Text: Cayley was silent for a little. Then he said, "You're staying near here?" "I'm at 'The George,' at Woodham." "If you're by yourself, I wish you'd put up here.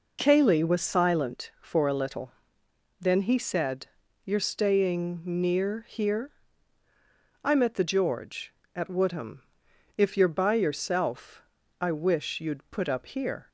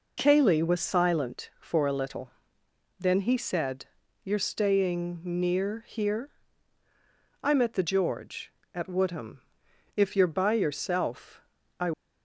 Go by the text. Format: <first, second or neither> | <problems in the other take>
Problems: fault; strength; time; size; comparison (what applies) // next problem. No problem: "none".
first | stops before "wish you'd put up here"; at 11.9 s